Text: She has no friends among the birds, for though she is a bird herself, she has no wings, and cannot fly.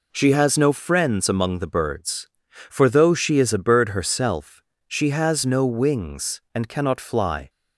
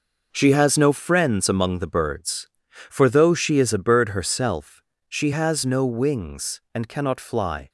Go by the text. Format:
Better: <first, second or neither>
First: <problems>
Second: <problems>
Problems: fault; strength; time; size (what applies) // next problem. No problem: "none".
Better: first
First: none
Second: gets quieter; strong; throughout; 9 dB